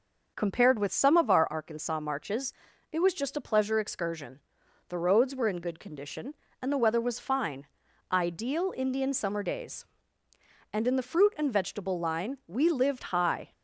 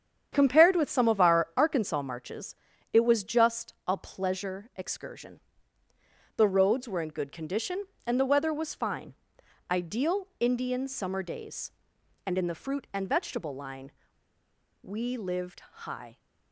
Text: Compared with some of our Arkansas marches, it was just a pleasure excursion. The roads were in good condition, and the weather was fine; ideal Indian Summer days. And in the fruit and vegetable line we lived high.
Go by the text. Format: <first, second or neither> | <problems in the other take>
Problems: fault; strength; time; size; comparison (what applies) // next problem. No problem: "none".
first | starts louder than the rest; strong; until 1.3 s; 8.5 dB; noticeable in the first // pauses between "just" and "a"; slight; at 3.7 s; 0.16 s long // pauses between "line" and "we"; noticeable; at 13.9 s; 0.90 s long // pauses between "lived" and "high"; slight; at 15.6 s; 0.22 s long